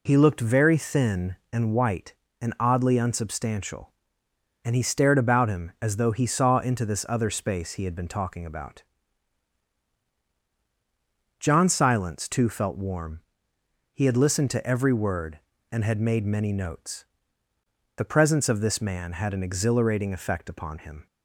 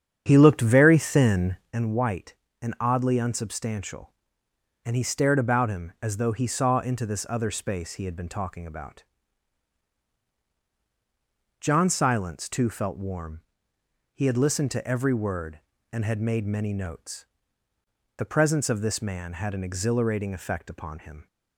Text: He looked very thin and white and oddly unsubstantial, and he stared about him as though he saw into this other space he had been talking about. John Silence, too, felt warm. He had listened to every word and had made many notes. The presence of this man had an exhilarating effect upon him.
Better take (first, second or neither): first